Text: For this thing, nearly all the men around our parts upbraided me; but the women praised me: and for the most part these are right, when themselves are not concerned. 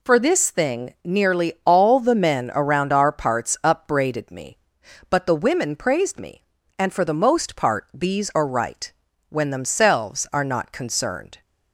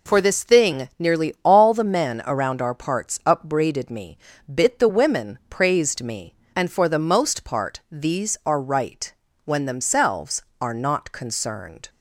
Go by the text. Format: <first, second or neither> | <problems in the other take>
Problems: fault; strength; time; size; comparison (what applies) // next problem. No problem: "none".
first | says "bit" for "but"; at 4.4 s